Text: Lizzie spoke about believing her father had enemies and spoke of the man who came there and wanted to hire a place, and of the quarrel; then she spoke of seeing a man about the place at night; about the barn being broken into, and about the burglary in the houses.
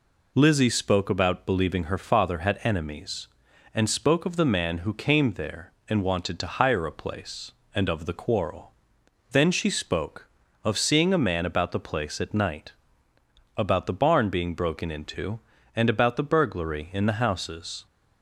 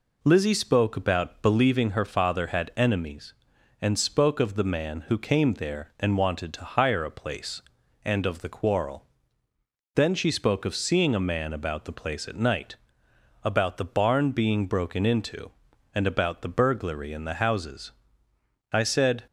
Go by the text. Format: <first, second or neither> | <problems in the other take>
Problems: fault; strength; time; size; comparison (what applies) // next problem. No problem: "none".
first | goes on to say "I said"; from 18.7 s on; 0.52 s long